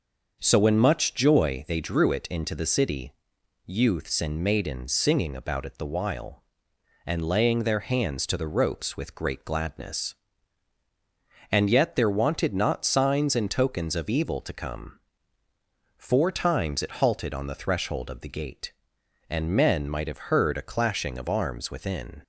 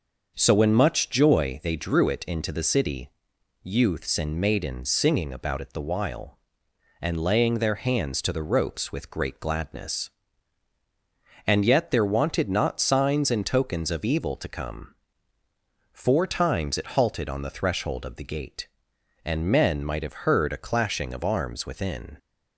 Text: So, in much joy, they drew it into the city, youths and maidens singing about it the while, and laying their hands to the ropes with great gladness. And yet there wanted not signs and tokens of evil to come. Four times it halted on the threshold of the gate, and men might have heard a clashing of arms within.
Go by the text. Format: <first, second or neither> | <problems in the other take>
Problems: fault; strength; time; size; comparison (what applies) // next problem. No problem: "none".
neither | starts louder than the rest; noticeable; the same in both